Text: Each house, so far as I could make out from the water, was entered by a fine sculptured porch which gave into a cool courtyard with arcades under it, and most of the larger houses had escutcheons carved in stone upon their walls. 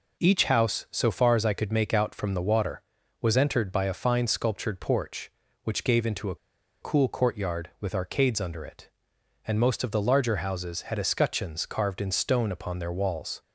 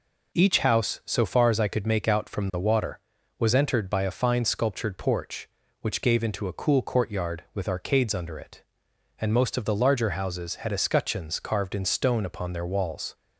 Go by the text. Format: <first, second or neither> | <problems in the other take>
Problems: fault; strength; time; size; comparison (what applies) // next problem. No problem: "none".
second | pauses between "a" and "cool"; noticeable; at 6.3 s; 0.46 s long